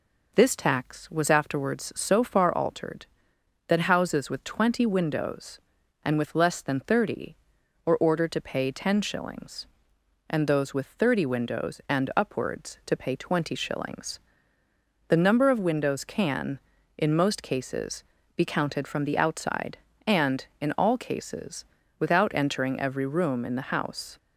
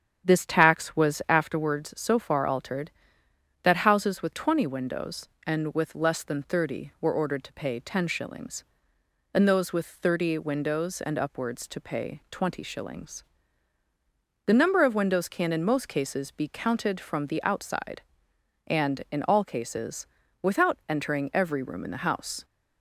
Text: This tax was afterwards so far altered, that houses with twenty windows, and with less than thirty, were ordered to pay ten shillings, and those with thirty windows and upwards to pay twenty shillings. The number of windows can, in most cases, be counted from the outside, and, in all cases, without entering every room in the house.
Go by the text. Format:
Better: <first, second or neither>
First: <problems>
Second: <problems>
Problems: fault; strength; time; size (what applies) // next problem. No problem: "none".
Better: first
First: none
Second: starts louder than the rest; strong; until 1.6 s; 8.5 dB